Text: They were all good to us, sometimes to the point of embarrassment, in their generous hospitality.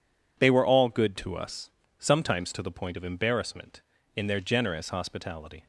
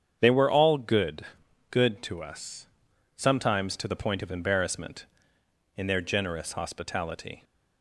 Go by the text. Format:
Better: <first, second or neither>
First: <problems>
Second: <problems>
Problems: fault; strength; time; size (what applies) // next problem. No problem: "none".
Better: first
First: none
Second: starts louder than the rest; strong; until 1.2 s; 8 dB // says "good" twice; at 1.7 s